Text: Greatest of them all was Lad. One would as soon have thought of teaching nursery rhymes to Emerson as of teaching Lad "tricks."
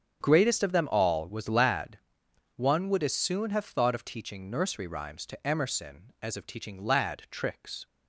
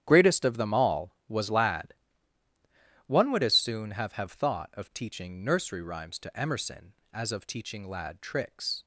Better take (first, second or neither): first